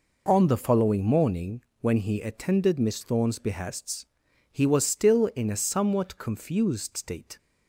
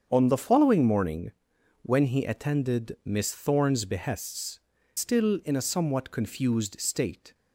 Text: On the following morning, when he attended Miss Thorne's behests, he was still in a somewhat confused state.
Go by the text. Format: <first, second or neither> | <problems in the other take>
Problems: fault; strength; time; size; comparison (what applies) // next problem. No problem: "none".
first | starts louder than the rest; strong; until 1.1 s; 7.5 dB // skips "he was"; at 4.7 s